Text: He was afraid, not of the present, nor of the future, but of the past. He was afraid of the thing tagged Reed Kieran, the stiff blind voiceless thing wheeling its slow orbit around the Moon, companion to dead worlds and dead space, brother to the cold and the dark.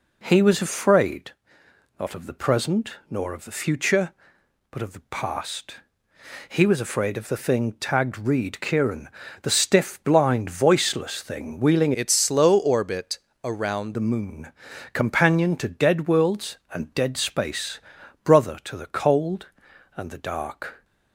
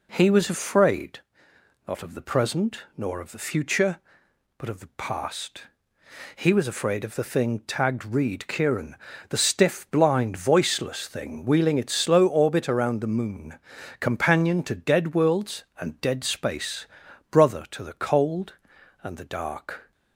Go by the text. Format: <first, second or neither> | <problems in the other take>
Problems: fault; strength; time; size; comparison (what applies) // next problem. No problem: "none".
second | changes voice from "its" to "around"; from 11.9 to 13.9 s; 2.0 s long // pauses between "orbit" and "around"; slight; at 13.1 s; 0.24 s long